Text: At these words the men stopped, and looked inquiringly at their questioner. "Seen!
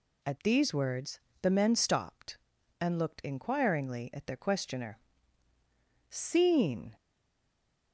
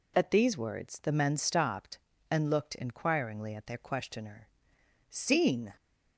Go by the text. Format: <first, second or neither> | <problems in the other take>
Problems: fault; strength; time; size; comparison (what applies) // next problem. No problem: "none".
second | pauses between "words" and "the"; slight; at 1.1 s; 0.24 s long // stays silent after the last word; slight; from 6.9 s on; 1.0 s long